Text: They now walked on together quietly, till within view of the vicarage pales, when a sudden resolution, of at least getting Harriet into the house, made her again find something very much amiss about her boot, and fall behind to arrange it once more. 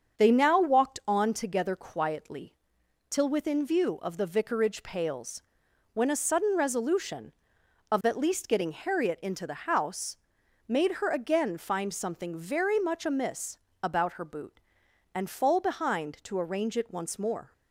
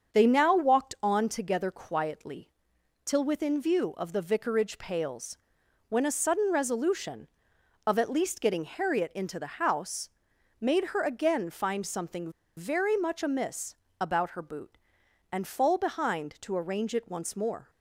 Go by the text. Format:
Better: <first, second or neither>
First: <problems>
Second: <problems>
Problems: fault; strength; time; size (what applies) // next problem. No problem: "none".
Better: first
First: starts louder than the rest; strong; until 1.2 s; 7 dB // pauses between "amiss" and "about"; slight; at 13.5 s; 0.24 s long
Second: starts louder than the rest; until 1.2 s; 7 dB // pauses between "something" and "very"; slight; at 12.2 s; 0.27 s long // pauses between "amiss" and "about"; slight; at 13.7 s; 0.24 s long